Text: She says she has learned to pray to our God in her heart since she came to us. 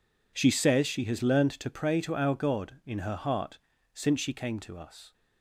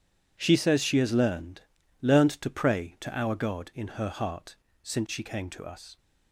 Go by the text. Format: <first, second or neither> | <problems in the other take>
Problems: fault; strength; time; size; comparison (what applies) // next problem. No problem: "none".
first | says "learned" twice; at 1.9 s // pauses between "heart" and "since"; slight; at 4.5 s; 0.30 s long; slight in the first